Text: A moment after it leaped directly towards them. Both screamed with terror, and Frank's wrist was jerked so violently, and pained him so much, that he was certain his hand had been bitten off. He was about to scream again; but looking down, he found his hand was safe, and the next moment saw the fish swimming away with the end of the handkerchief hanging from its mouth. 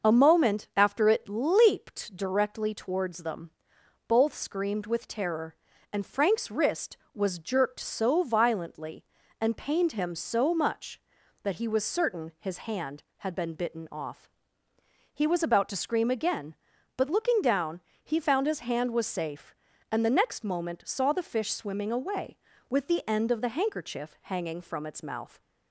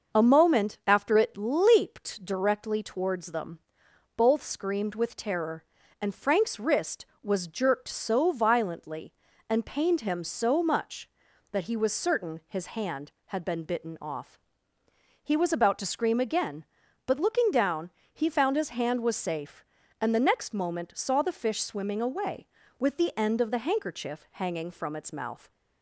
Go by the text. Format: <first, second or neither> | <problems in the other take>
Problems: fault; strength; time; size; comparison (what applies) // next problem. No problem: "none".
neither | starts louder than the rest; the same in both